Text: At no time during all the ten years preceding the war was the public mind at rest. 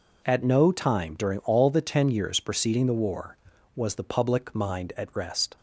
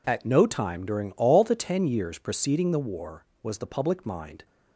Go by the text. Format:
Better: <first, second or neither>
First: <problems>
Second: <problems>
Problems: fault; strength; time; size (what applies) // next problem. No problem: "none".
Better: first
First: none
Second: stops before "at rest"; at 4.4 s